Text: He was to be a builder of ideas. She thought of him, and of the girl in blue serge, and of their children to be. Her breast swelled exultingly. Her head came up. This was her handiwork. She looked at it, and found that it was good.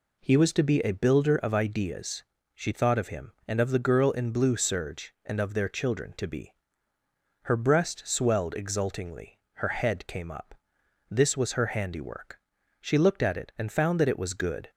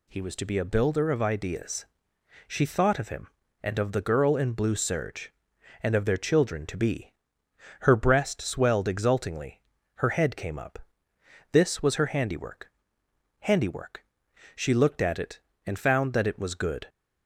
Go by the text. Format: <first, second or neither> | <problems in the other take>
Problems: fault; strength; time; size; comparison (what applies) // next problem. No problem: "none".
first | says "handiwork" twice; at 13.4 s